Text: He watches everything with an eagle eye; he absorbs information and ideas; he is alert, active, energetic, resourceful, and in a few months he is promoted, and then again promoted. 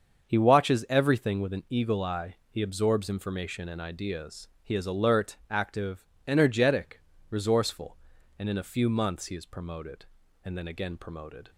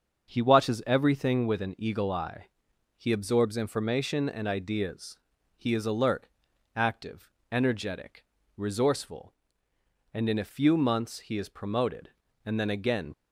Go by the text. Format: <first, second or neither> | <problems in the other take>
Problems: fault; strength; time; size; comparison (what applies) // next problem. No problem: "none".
first | starts louder than the rest; until 1.3 s; 6.5 dB; also in the first // stops before "promoted"; at 13.1 s